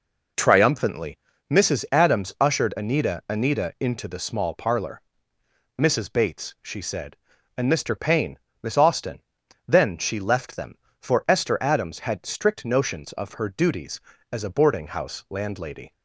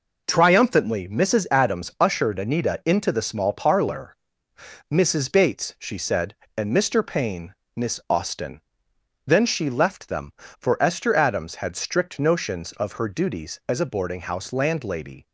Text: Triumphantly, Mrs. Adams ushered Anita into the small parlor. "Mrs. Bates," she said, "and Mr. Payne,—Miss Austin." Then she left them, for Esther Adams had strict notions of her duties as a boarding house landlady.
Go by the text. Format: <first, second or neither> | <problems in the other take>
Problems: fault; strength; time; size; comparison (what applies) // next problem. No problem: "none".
second | says "Anita" twice; at 3.2 s